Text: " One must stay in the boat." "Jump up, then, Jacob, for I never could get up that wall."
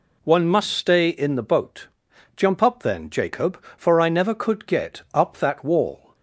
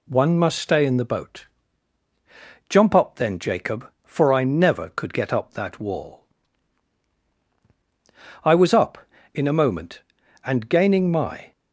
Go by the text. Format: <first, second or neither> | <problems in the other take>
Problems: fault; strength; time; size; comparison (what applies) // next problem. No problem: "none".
first | goes on to say "I was up In a moment and gaining my"; strong; from 8.4 s on; 3.1 s long